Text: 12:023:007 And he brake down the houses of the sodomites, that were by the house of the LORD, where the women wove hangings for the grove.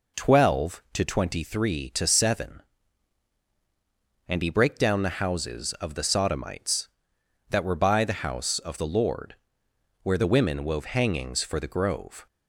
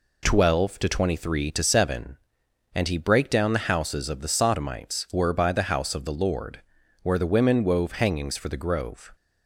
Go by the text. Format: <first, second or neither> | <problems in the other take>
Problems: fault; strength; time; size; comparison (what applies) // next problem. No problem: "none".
first | skips "that"; at 5.0 s